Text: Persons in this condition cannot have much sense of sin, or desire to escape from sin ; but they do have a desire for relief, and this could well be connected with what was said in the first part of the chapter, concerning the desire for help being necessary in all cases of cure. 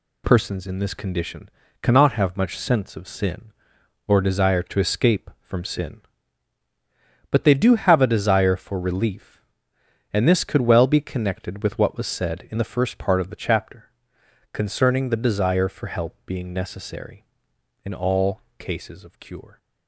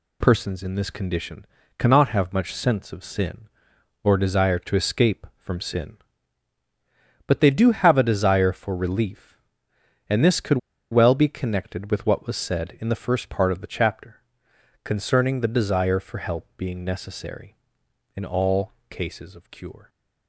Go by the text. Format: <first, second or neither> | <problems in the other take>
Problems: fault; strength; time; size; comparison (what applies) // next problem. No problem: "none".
first | pauses between "condition" and "cannot"; slight; at 1.4 s; 0.34 s long; slight in the first // pauses between "could" and "well"; slight; at 10.5 s; 0.33 s long // pauses between "all" and "cases"; slight; at 18.7 s; 0.18 s long; slight in the first